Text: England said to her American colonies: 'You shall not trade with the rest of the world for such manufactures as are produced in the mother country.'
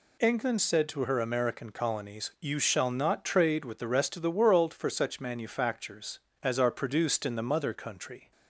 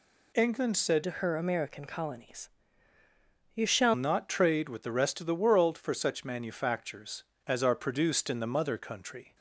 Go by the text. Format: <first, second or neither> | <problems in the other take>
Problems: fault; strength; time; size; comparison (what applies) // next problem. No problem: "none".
first | changes voice from "to" to "shall"; from 1.0 to 3.9 s; 2.9 s long